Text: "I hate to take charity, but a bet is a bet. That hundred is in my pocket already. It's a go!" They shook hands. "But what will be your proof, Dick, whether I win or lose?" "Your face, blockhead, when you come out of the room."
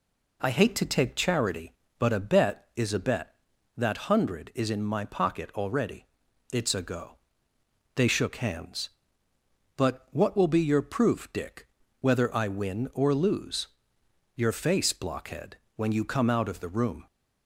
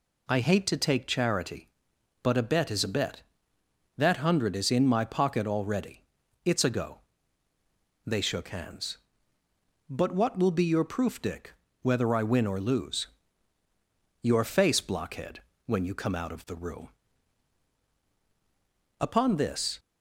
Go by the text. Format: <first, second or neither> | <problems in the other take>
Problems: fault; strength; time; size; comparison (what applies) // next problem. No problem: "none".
first | goes on to say "Upon this"; noticeable; from 18.9 s on; 0.80 s long